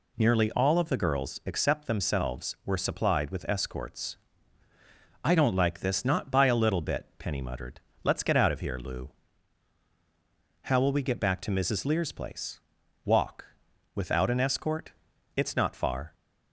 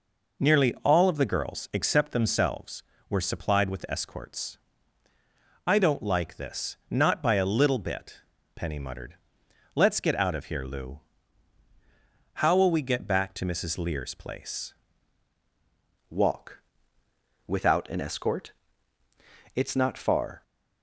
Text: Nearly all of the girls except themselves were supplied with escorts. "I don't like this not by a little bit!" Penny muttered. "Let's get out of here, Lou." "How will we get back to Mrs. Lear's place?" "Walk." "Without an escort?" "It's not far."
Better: first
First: none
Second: changes voice at "Walk"; from 16.1 s on; 4.3 s long

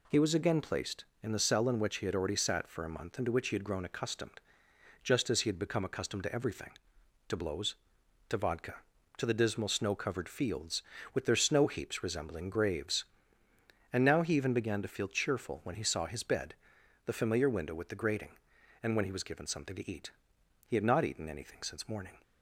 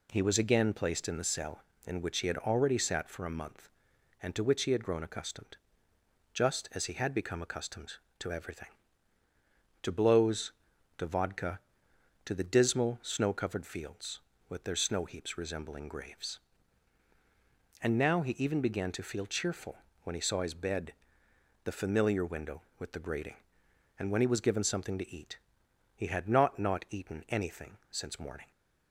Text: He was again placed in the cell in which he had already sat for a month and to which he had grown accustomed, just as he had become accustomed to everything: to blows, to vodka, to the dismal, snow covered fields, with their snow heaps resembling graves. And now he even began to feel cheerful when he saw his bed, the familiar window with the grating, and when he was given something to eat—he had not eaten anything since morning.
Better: first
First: none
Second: pauses between "cheerful" and "when"; slight; at 19.7 s; 0.24 s long // says "not" twice; at 26.5 s // pauses between "anything" and "since"; slight; at 27.7 s; 0.16 s long

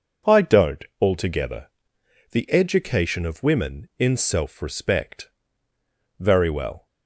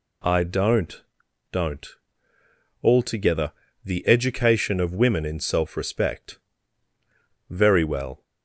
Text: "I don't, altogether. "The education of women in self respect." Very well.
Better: first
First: none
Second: says "don't" twice; at 1.5 s

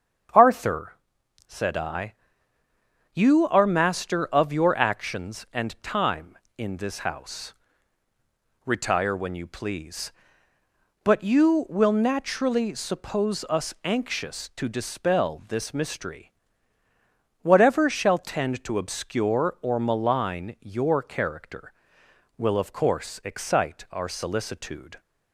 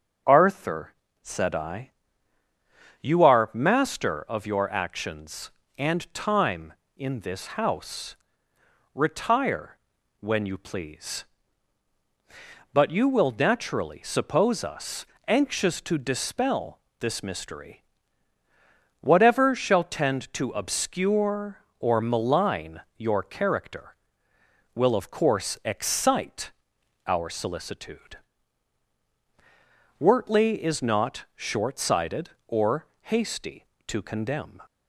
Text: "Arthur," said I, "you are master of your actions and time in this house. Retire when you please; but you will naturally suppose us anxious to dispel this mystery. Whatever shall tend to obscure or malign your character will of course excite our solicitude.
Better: first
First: starts louder than the rest; strong; until 1.9 s; 7.5 dB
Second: starts louder than the rest; until 1.5 s; 6.5 dB // pauses between "Retire" and "when"; at 9.7 s; 0.44 s long // pauses between "us" and "anxious"; slight; at 15.0 s; 0.22 s long // pauses between "dispel" and "this"; slight; at 16.7 s; 0.20 s long // pauses between "malign" and "your"; slight; at 22.8 s; 0.16 s long // pauses between "excite" and "our"; noticeable; at 26.5 s; 0.54 s long // goes on to say "Wortley is not short sighted or hasty to condemn"; strong; from 29.9 s on; 4.6 s long

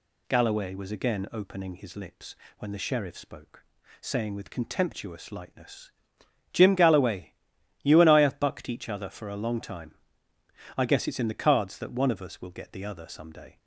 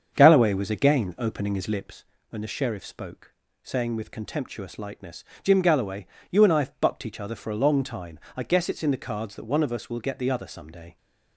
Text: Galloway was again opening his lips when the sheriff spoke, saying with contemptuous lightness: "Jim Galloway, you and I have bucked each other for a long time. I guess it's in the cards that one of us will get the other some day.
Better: first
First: pauses between "lips" and "when"; slight; at 2.3 s; 0.24 s long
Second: starts louder than the rest; strong; until 2.0 s; 7 dB // pauses between "lips" and "when"; slight; at 2.0 s; 0.24 s long

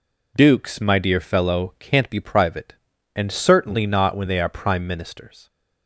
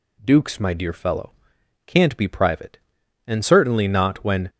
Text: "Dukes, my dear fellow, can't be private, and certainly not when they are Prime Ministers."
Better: first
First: none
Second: stops before "they are Prime Ministers"; at 4.4 s

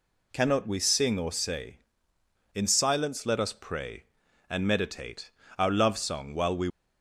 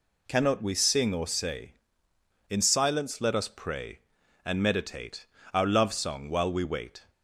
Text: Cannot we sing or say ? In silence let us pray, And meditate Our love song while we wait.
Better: second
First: pauses between "meditate" and "Our"; slight; at 5.3 s; 0.26 s long // stops before "wait"; at 6.6 s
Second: pauses between "meditate" and "Our"; slight; at 5.2 s; 0.26 s long

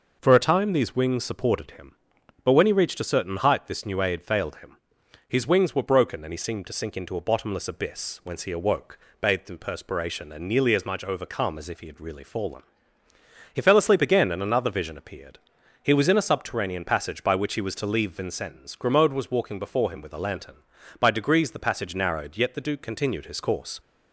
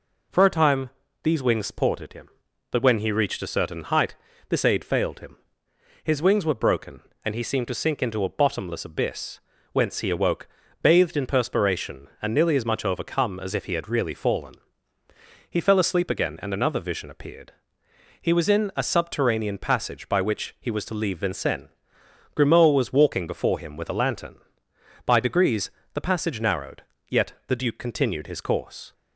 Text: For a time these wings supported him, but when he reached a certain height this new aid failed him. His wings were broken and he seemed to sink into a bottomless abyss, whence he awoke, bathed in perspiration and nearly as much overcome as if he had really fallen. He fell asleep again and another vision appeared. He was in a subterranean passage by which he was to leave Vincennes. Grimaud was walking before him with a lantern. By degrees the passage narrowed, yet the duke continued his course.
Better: first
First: none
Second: pauses between "time" and "these"; slight; at 0.8 s; 0.34 s long // pauses between "height" and "this"; slight; at 4.1 s; 0.34 s long // skips "new"; at 4.6 s // pauses between "degrees" and "the"; slight; at 25.7 s; 0.22 s long

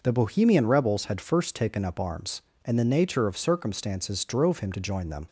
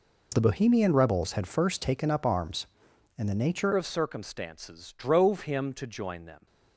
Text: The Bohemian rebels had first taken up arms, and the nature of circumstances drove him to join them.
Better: first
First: none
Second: changes voice at "of"; from 3.7 s on; 2.7 s long

